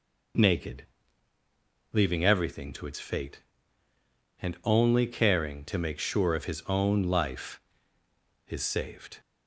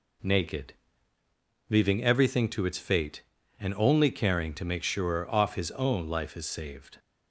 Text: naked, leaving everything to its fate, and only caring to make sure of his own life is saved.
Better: first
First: none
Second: says "off" for "of"; at 5.3 s

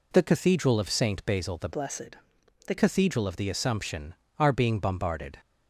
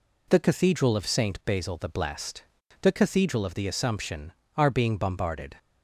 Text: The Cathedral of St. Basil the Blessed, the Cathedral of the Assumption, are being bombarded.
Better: second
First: changes voice from "Blessed" to "the"; from 1.7 to 2.7 s; 1.0 s long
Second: none

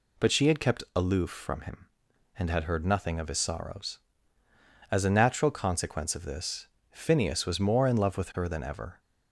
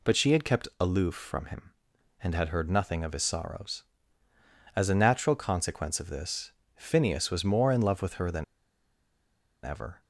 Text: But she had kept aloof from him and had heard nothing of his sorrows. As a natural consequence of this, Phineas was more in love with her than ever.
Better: first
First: none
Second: pauses between "than" and "ever"; at 8.4 s; 1.2 s long

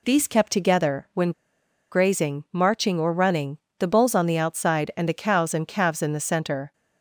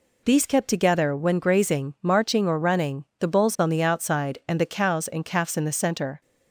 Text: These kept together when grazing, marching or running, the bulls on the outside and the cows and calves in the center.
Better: second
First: pauses between "when" and "grazing"; noticeable; at 1.3 s; 0.60 s long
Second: none

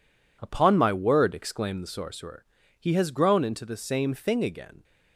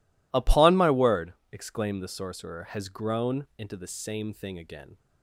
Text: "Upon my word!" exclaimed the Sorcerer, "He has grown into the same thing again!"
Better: first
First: none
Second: skips "He"; at 2.6 s

